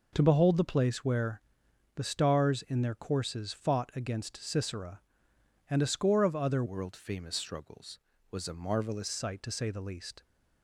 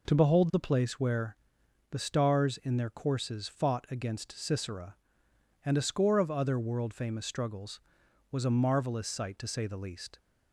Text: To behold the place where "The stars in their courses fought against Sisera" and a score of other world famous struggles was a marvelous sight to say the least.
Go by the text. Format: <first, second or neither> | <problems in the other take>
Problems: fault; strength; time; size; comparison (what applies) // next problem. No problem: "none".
second | pauses between "where" and "The"; noticeable; at 1.4 s; 0.54 s long; noticeable in the second // changes voice from "world" to "marvelous"; from 6.6 to 9.0 s; 2.4 s long